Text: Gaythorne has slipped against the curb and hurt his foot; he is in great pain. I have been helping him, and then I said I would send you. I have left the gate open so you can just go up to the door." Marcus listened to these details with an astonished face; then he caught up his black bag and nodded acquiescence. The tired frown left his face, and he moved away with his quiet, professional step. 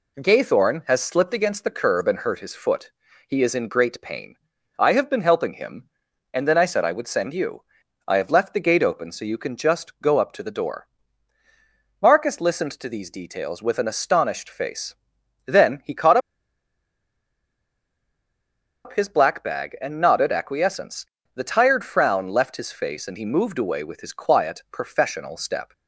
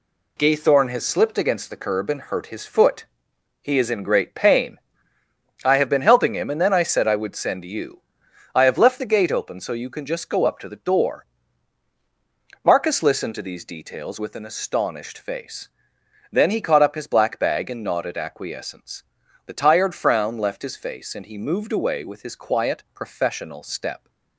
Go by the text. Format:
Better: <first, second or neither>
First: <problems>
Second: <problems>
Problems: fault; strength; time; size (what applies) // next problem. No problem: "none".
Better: second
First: pauses between "caught" and "up"; strong; at 16.1 s; 2.6 s long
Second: none